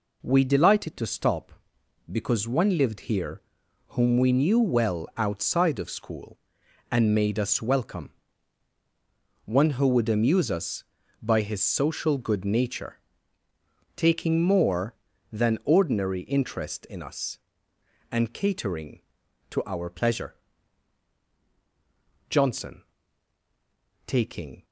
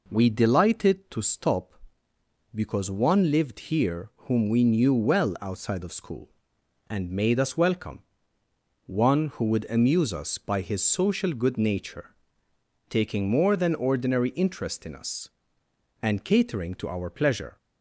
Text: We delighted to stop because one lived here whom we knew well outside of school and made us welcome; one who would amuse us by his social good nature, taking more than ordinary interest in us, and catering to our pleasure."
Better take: second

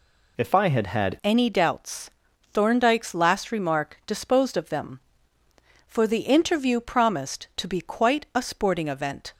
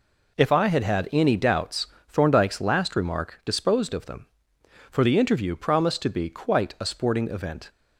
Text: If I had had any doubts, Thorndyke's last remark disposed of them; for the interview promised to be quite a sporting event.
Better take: second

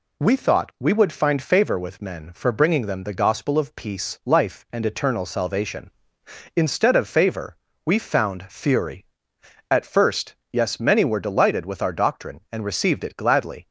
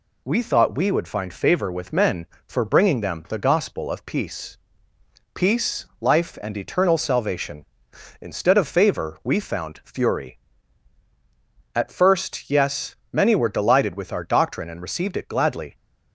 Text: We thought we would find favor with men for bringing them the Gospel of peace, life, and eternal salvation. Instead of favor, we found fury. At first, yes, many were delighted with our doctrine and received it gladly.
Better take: first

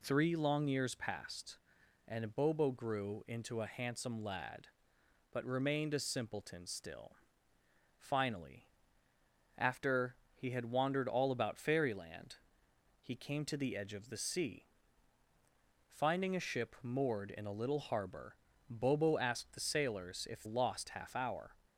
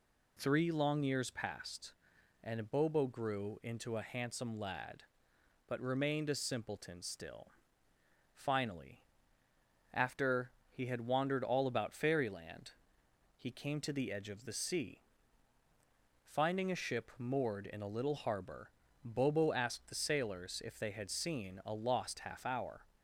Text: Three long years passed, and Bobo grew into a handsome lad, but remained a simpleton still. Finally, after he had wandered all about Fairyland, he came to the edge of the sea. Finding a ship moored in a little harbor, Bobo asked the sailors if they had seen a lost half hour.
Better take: second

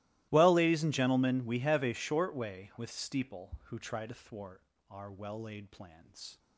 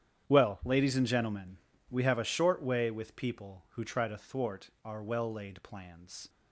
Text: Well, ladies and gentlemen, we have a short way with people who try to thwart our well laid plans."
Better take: second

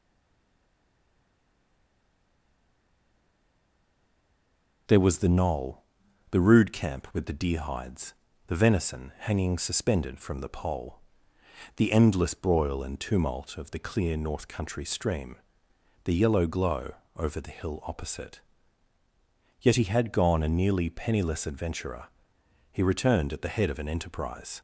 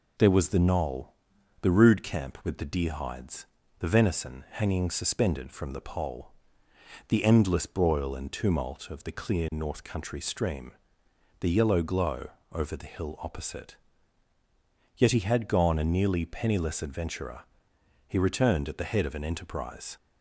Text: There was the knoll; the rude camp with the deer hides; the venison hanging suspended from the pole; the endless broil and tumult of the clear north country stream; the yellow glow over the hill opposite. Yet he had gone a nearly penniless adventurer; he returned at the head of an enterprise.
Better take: second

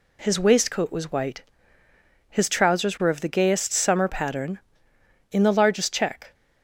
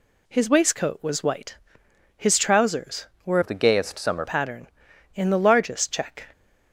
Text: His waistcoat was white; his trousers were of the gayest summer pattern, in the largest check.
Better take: first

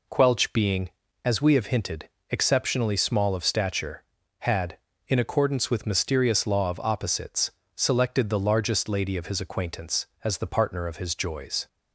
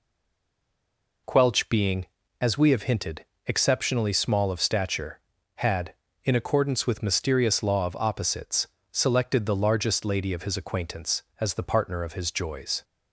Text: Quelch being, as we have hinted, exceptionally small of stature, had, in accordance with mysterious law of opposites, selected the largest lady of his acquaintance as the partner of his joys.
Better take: first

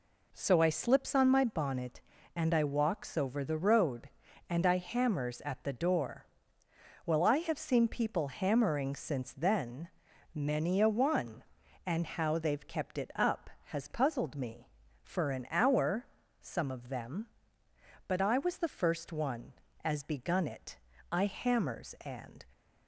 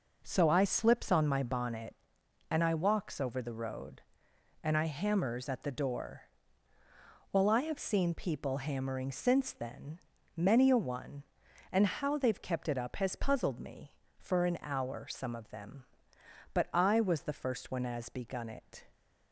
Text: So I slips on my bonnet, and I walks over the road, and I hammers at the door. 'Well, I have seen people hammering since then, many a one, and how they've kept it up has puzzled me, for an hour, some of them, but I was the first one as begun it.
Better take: second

